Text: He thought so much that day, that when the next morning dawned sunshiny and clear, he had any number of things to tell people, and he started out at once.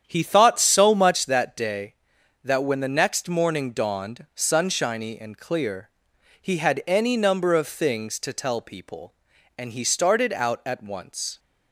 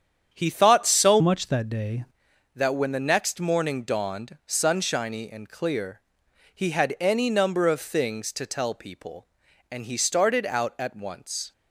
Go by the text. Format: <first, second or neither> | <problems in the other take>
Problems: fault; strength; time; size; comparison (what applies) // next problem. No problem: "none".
first | starts louder than the rest; strong; until 1.3 s; 8.5 dB; strong in the first // changes voice from "much" to "day"; from 1.1 to 2.0 s; 0.9 s long